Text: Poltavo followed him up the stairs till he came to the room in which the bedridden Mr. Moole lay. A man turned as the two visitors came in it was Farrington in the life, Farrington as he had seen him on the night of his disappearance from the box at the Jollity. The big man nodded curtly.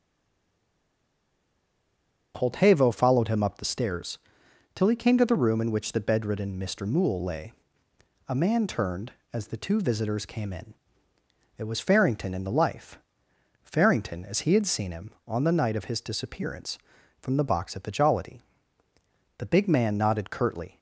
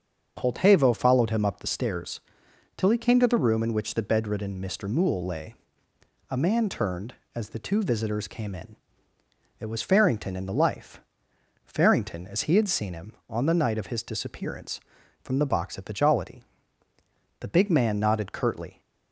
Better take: second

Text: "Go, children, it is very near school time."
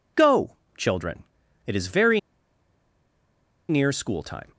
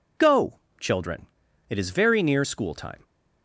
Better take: second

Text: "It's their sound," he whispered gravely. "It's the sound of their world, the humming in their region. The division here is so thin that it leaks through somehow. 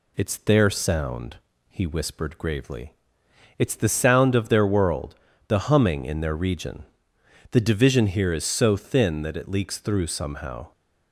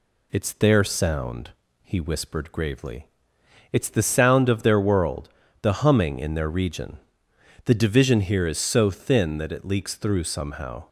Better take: neither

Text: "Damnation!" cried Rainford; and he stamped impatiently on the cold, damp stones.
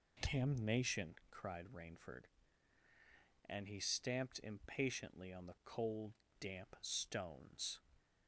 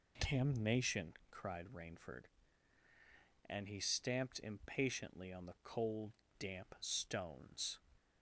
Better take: neither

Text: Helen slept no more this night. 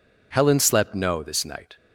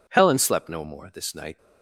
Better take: second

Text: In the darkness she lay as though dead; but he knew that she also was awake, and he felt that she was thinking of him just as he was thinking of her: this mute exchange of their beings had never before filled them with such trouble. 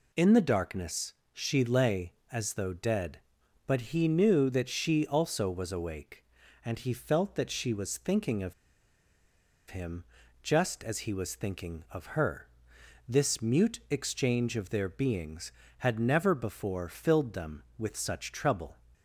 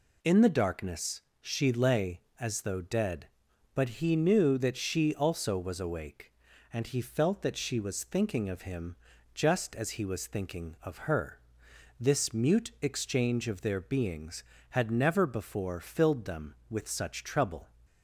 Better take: second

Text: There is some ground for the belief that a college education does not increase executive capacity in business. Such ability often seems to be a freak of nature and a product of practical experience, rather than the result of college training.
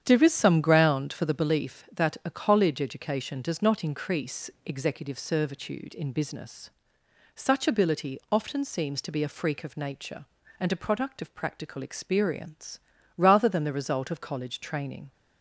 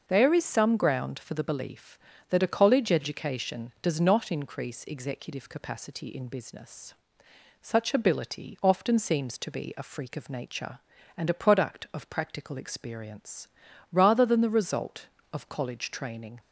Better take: second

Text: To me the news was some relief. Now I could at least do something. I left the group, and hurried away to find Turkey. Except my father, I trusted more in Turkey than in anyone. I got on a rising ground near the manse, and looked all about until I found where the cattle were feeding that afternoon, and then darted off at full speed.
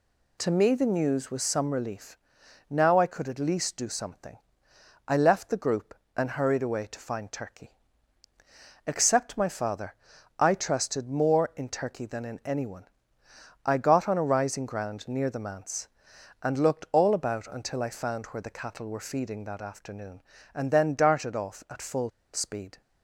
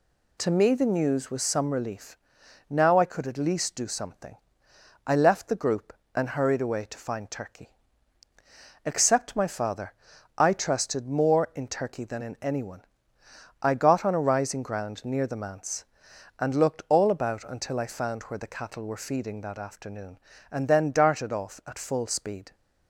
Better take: second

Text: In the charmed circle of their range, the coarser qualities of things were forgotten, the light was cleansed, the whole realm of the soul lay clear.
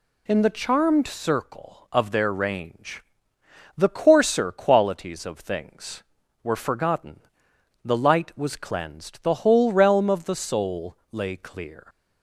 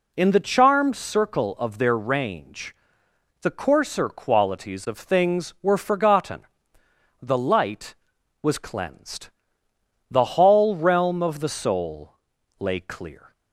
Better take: first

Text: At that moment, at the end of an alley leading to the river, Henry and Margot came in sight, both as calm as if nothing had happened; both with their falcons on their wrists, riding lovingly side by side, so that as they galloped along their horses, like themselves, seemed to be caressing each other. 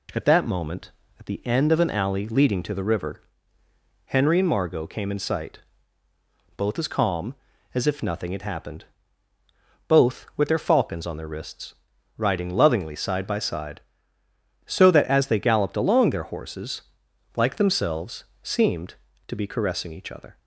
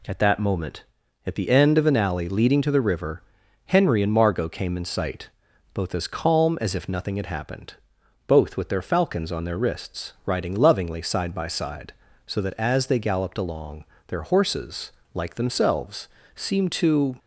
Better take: first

